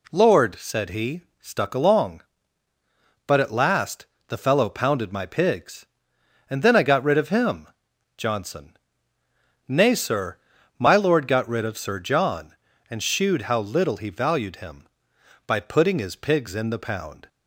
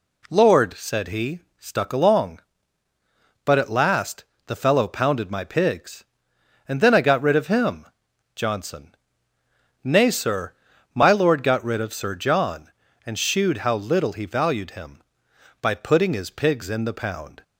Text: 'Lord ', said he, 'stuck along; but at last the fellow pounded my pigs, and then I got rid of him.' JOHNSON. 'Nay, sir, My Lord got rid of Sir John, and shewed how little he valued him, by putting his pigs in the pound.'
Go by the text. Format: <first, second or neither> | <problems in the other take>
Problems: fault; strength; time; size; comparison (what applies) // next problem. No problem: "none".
neither | pauses between "last" and "the"; slight; the same in both